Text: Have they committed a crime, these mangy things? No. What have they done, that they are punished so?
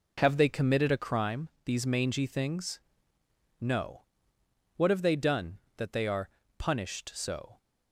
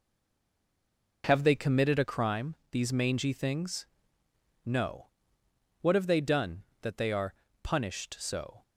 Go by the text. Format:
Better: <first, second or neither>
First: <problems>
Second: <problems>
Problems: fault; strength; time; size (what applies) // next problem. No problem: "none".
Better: first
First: pauses between "are" and "punished"; slight; at 6.2 s; 0.30 s long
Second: stays silent before the first word; noticeable; until 1.2 s; 1.2 s long // pauses between "are" and "punished"; slight; at 7.3 s; 0.30 s long